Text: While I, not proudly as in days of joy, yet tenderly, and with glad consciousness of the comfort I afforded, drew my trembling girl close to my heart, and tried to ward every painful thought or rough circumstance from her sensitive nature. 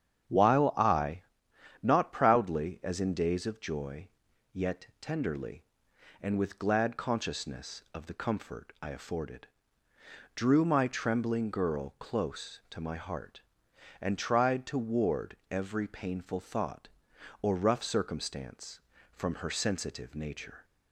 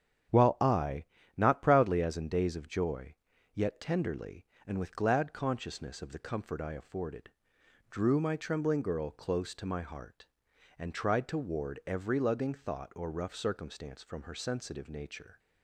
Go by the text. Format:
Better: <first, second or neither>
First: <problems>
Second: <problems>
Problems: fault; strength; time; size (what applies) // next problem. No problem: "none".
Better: first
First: starts louder than the rest; strong; until 1.9 s; 8.5 dB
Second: starts louder than the rest; strong; until 1.6 s; 8.5 dB // says "lugging" for "painful"; at 12.1 s